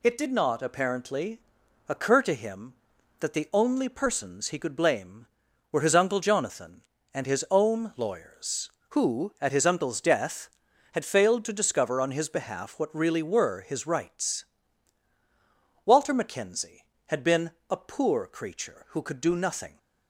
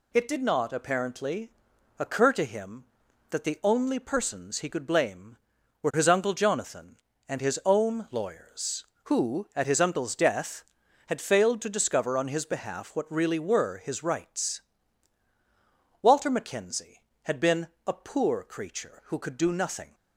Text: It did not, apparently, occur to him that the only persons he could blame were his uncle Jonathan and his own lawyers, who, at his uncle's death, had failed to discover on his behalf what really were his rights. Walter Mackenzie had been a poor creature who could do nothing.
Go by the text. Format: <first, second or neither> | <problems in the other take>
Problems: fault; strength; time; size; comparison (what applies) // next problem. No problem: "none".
neither | pauses between "been" and "a"; slight; the same in both